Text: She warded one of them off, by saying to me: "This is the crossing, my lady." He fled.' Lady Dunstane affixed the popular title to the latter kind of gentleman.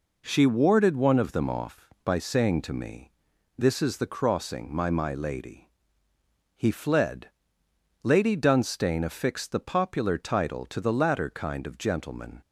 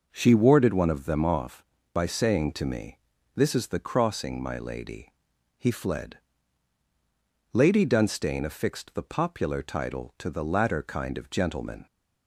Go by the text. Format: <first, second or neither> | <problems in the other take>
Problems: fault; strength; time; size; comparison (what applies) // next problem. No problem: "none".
second | says "my" twice; at 4.8 s